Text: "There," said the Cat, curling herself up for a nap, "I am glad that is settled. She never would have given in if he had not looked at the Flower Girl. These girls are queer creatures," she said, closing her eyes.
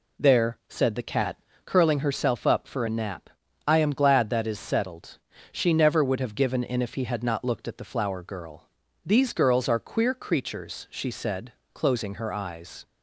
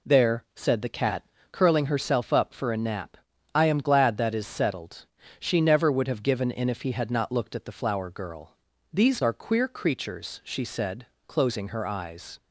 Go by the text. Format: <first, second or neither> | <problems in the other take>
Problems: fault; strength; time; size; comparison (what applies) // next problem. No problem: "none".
first | skips "girls"; at 9.2 s